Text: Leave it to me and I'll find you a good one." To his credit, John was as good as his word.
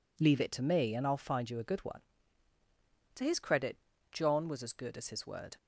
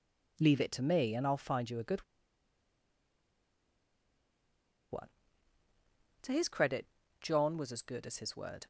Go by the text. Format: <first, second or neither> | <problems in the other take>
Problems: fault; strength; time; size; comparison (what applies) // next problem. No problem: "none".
first | pauses between "good" and "one"; strong; at 2.0 s; 2.8 s long